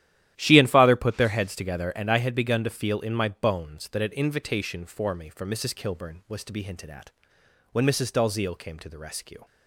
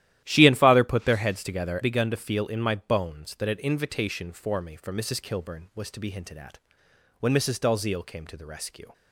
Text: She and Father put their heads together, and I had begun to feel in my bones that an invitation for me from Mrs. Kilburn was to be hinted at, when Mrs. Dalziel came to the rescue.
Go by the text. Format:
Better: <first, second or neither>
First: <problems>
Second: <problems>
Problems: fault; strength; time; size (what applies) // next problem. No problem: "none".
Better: first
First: starts louder than the rest; strong; until 1.3 s; 12 dB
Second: starts louder than the rest; strong; until 1.2 s; 13 dB // skips "and I had"; at 1.7 s